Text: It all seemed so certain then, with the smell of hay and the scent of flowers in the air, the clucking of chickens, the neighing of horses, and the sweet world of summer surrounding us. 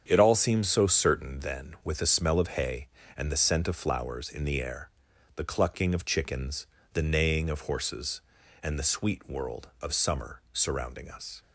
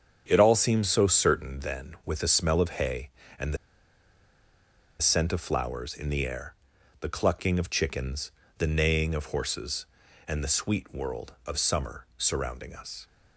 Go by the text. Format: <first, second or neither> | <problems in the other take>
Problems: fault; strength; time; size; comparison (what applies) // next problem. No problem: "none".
first | starts louder than the rest; strong; until 1.2 s; 7.5 dB; strong in the first // pauses between "the" and "scent"; strong; at 3.5 s; 1.4 s long